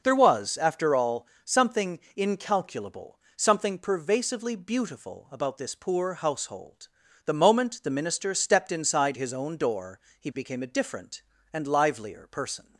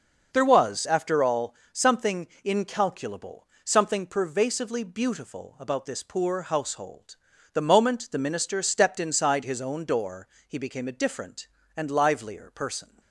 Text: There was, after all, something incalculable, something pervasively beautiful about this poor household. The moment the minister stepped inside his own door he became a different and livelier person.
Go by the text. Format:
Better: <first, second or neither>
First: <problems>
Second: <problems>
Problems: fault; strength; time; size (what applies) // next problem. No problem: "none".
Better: neither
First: starts louder than the rest; noticeable; until 1.0 s; 6 dB // pauses between "something" and "incalculable"; slight; at 1.9 s; 0.16 s long // pauses between "door" and "he"; slight; at 9.9 s; 0.20 s long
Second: starts louder than the rest; noticeable; until 1.3 s; 6 dB // pauses between "something" and "incalculable"; slight; at 2.2 s; 0.16 s long // pauses between "door" and "he"; slight; at 10.2 s; 0.20 s long